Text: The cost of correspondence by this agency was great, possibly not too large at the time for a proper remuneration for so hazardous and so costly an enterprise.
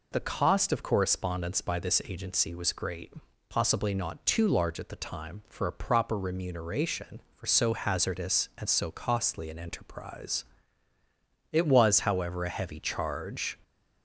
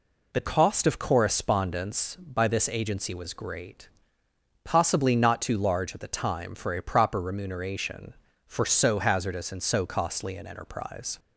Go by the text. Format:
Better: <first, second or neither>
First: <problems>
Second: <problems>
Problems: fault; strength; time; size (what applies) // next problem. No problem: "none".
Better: second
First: goes on to say "It was however a heavy charge"; strong; from 11.5 s on; 2.0 s long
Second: none